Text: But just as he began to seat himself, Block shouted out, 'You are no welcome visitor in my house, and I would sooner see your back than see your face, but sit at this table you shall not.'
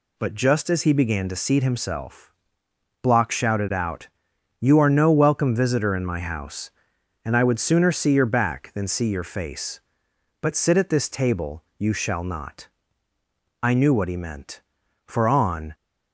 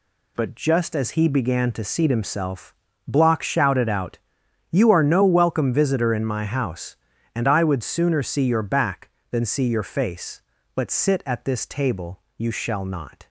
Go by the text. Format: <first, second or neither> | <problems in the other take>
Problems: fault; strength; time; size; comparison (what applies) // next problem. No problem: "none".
second | pauses between "table" and "you"; slight; at 11.6 s; 0.16 s long; slight in the second // goes on to say "I knew what he meant for on"; strong; from 13.6 s on; 2.1 s long